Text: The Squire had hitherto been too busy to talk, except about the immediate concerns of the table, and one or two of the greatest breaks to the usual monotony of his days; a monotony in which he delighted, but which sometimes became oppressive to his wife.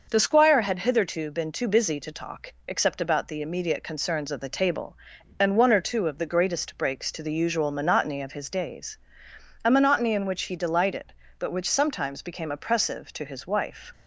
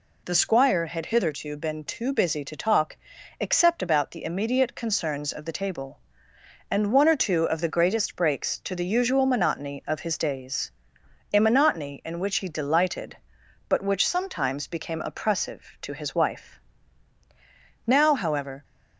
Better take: first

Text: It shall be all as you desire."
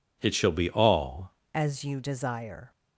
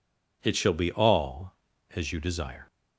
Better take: second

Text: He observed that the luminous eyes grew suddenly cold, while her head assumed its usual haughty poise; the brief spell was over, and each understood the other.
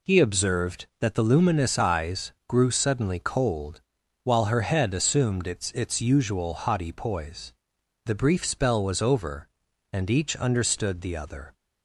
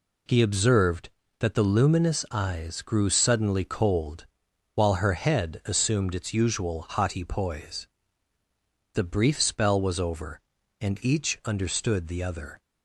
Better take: second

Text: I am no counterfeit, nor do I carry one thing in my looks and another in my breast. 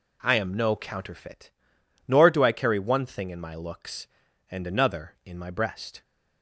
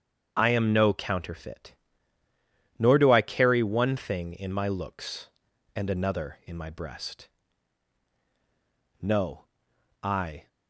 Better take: first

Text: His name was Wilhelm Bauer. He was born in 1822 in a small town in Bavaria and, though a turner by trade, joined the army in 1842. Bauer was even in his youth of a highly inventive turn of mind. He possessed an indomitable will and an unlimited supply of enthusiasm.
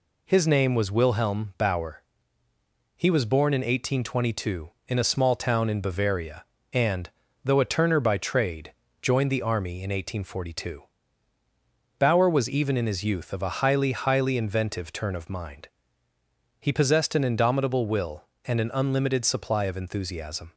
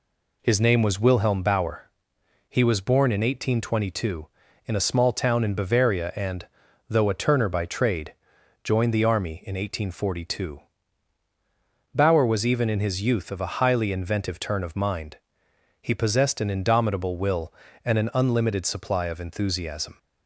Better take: second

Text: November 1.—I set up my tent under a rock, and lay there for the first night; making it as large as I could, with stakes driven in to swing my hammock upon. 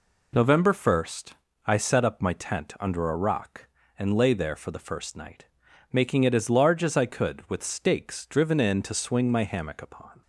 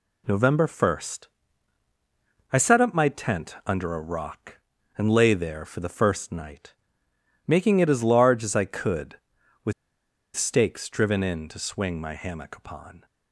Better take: first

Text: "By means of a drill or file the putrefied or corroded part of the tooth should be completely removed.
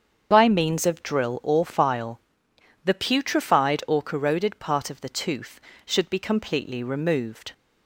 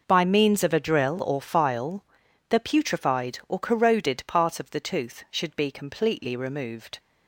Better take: second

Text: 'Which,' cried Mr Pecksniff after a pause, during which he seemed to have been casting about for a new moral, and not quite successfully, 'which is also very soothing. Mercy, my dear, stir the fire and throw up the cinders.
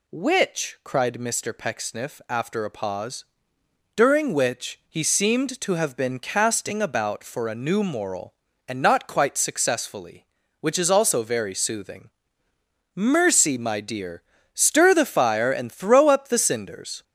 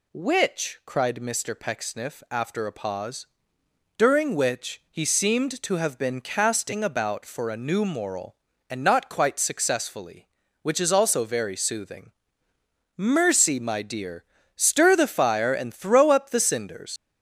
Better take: first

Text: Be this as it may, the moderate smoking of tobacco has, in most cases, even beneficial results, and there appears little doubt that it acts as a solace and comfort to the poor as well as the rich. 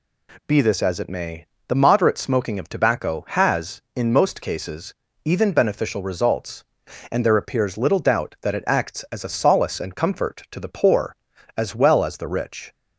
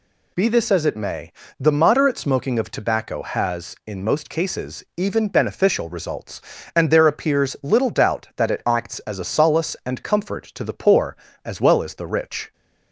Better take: neither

